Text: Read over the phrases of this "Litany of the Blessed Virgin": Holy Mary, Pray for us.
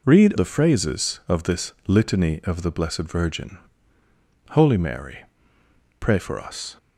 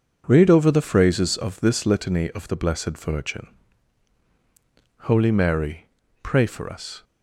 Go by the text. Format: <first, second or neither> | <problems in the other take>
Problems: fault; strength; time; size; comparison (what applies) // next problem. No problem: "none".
second | skips "over"; at 0.3 s